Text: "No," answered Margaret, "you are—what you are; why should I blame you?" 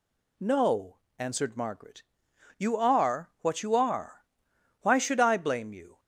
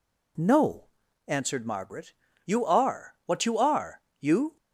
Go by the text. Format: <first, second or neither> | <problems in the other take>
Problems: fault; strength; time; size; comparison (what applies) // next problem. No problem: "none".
first | skips "why should I blame"; at 4.1 s